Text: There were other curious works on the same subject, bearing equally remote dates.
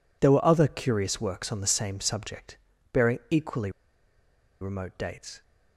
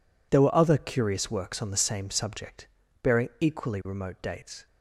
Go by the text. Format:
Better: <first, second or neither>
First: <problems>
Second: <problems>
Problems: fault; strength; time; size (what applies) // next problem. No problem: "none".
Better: second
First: pauses between "equally" and "remote"; noticeable; at 3.6 s; 0.91 s long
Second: none